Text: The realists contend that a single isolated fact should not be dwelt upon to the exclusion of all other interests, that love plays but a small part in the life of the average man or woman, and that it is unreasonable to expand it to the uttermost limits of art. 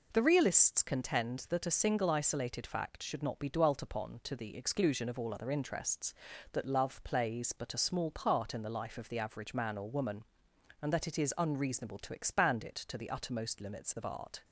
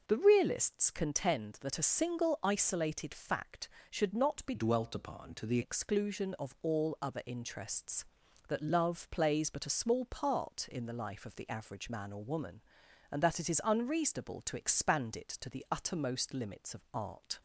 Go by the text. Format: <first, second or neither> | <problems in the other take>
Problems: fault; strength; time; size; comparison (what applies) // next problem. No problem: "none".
first | changes voice from "dwelt" to "the"; from 4.5 to 5.5 s; 1.0 s long